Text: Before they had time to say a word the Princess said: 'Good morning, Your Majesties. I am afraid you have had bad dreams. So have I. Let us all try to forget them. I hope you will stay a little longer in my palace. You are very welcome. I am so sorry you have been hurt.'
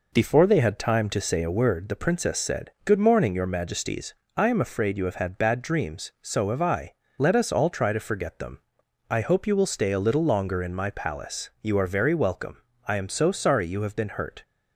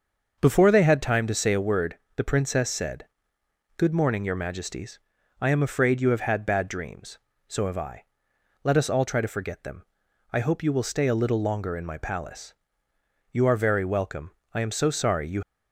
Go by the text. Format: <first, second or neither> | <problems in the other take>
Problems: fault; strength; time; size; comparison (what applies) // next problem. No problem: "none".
first | starts louder than the rest; until 1.4 s; 6.5 dB // pauses between "word" and "the"; slight; at 1.9 s; 0.16 s long // stops before "have been hurt"; at 15.4 s